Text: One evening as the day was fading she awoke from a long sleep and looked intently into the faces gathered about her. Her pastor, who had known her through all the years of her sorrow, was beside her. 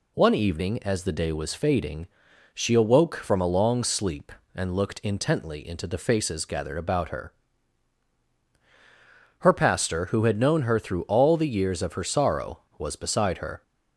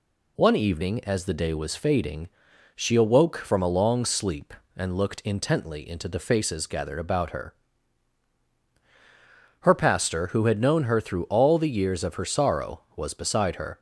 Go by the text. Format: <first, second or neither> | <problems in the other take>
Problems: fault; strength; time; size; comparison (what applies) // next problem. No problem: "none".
neither | pauses between "fading" and "she"; noticeable; the same in both